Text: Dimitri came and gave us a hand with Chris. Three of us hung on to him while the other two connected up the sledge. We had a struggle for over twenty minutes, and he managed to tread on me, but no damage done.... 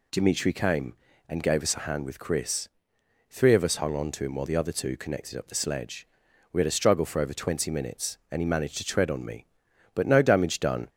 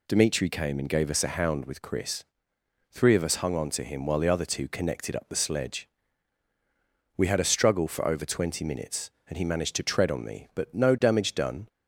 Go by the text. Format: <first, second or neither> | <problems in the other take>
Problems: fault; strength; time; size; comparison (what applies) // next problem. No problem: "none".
first | says "hound" for "hand"; at 1.2 s